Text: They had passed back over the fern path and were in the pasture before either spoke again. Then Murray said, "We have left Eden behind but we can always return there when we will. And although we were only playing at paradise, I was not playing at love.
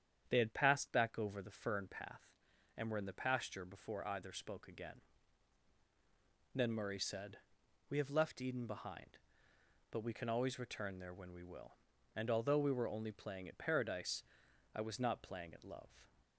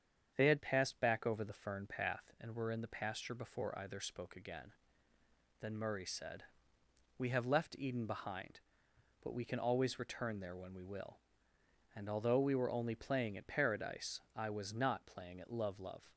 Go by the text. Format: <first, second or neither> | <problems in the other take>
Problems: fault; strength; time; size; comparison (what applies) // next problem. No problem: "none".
first | starts louder than the rest; strong; until 1.3 s; 8 dB; strong in the first // says "love" twice; at 15.7 s